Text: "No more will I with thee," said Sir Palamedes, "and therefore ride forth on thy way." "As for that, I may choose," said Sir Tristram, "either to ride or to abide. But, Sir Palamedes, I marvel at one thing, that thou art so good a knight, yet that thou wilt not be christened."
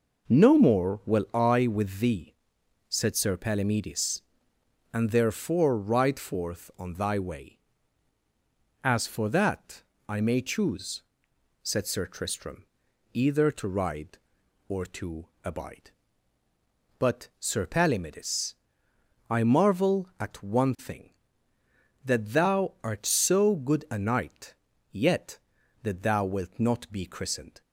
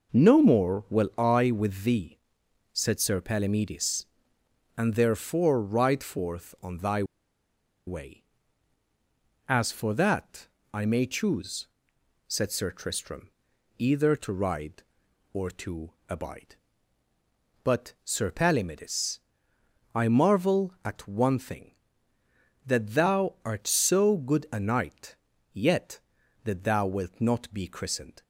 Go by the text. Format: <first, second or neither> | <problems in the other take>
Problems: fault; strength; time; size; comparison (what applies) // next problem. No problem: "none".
first | pauses between "thy" and "way"; noticeable; at 7.0 s; 0.83 s long // pauses between "to" and "abide"; slight; at 15.9 s; 0.16 s long; slight in the first